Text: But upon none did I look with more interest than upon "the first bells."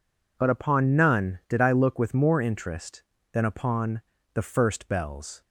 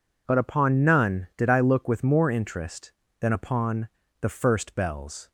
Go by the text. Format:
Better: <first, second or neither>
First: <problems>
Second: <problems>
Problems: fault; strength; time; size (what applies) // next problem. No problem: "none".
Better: neither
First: pauses between "upon" and "the"; slight; at 4.0 s; 0.32 s long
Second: pauses between "upon" and "the"; slight; at 3.8 s; 0.32 s long